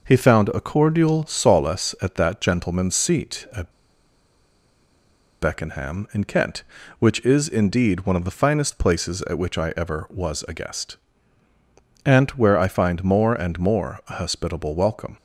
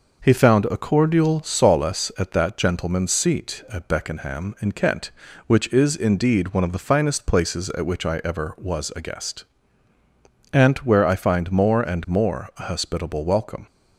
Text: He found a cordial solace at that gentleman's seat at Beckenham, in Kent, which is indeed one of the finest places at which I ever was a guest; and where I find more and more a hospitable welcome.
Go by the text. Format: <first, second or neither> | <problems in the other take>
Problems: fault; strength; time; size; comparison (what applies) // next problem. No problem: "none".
second | pauses between "at" and "Beckenham"; strong; at 3.7 s; 1.6 s long